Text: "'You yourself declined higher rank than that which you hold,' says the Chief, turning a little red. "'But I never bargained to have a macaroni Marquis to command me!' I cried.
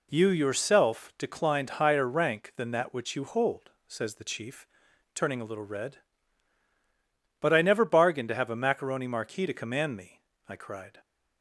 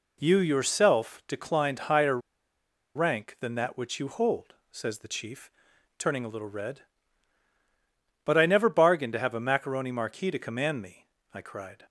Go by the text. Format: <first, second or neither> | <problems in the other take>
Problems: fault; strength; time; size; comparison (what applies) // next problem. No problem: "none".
first | pauses between "higher" and "rank"; noticeable; at 2.1 s; 0.77 s long